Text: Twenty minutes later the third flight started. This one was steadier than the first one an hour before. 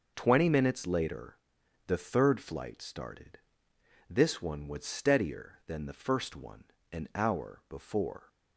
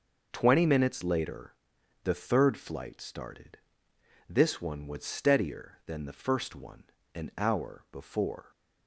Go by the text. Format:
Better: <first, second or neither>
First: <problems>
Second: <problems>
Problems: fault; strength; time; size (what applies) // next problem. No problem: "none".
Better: neither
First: pauses between "later" and "the"; noticeable; at 1.3 s; 0.50 s long // pauses between "one" and "an"; slight; at 6.6 s; 0.28 s long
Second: pauses between "later" and "the"; noticeable; at 1.5 s; 0.50 s long // pauses between "one" and "an"; slight; at 6.8 s; 0.31 s long